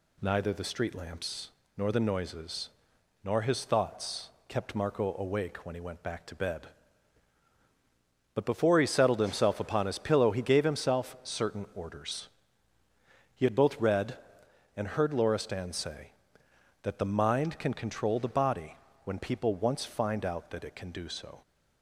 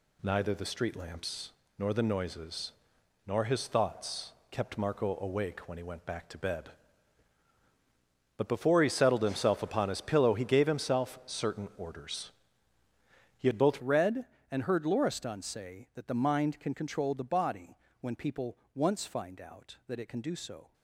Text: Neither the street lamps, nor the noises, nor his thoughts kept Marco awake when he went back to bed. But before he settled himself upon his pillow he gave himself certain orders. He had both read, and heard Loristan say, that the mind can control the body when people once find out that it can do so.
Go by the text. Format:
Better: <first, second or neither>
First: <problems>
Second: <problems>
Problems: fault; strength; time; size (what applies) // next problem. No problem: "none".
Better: first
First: pauses between "thoughts" and "kept"; slight; at 4.2 s; 0.18 s long // pauses between "body" and "when"; slight; at 18.7 s; 0.28 s long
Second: pauses between "thoughts" and "kept"; slight; at 4.3 s; 0.18 s long // changes voice at "read"; from 13.8 s on; 6.9 s long // pauses between "body" and "when"; slight; at 17.7 s; 0.24 s long // pauses between "people" and "once"; slight; at 18.5 s; 0.18 s long